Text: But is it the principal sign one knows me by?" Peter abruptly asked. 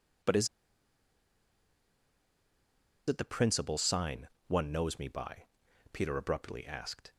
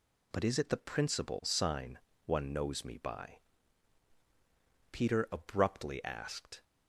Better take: second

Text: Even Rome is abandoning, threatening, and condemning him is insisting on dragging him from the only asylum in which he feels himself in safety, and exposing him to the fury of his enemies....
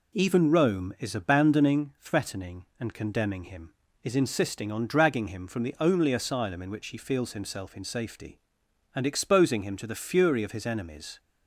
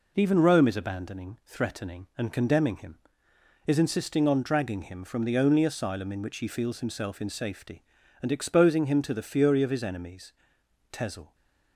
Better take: first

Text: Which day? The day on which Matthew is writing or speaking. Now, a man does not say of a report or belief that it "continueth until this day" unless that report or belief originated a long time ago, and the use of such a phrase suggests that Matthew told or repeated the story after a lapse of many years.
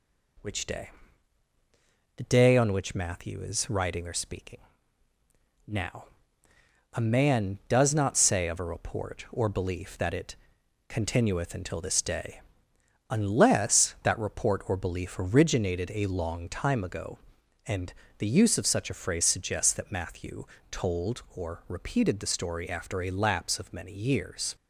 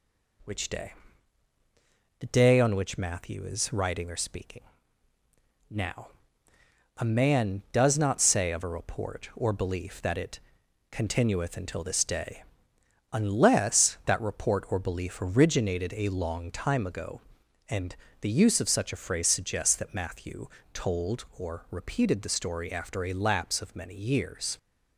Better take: neither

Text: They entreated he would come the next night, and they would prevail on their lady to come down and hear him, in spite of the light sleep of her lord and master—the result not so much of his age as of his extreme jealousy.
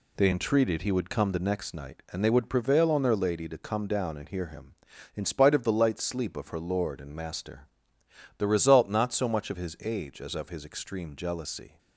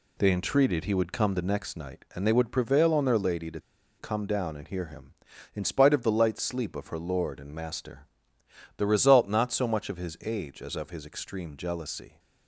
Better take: first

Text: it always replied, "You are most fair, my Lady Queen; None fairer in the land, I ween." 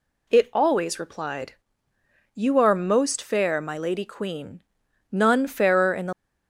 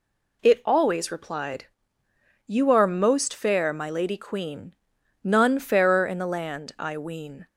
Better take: second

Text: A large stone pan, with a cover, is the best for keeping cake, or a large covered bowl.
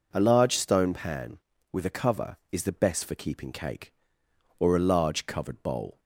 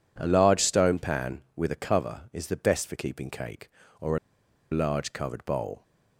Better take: first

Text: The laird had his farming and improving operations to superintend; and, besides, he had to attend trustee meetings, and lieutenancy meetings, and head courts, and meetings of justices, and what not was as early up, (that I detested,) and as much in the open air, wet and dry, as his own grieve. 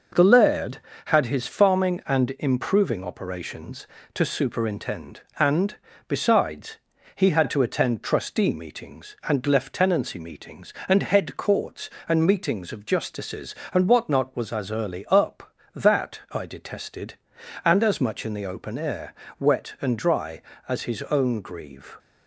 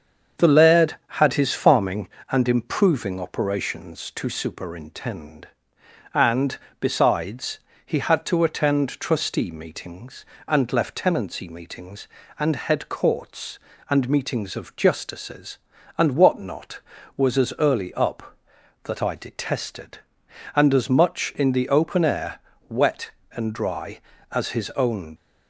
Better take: first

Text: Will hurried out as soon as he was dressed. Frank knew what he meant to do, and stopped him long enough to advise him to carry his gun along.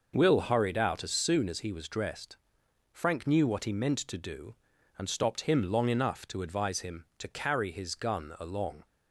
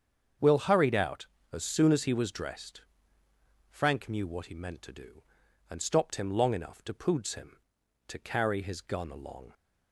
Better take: first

